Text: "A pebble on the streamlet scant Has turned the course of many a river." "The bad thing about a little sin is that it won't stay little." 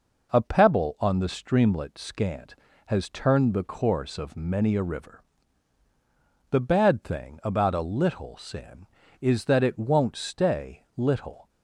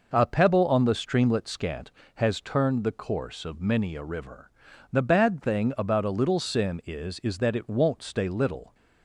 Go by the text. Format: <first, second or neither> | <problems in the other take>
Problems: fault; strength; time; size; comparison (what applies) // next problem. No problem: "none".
first | says "is" twice; at 7.2 s